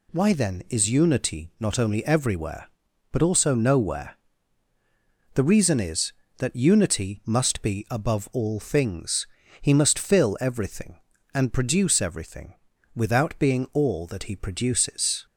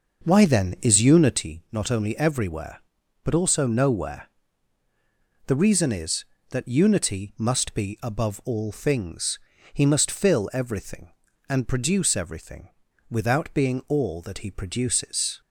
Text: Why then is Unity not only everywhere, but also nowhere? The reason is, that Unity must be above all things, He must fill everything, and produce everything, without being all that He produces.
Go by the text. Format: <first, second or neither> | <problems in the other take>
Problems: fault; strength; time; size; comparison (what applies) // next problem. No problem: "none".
first | starts louder than the rest; noticeable; until 1.5 s; 6 dB